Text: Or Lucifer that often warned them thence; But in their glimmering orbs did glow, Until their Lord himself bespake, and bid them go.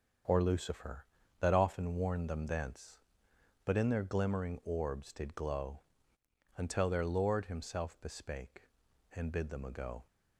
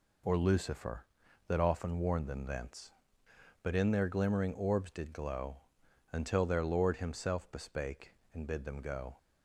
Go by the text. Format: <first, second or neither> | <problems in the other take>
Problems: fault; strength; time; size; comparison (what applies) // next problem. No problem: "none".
second | starts louder than the rest; until 1.6 s; 7 dB // says "ago" for "go"; at 9.6 s